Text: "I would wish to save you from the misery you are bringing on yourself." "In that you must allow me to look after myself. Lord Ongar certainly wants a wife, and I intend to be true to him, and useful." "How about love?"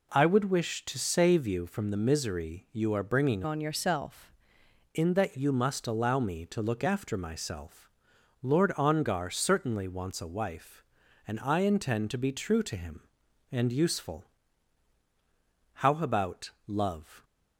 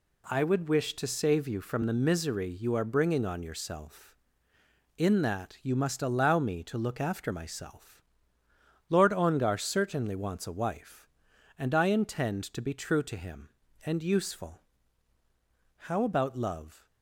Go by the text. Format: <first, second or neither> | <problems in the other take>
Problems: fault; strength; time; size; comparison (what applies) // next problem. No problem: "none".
second | changes voice from "on" to "yourself"; from 3.4 to 4.2 s; 0.8 s long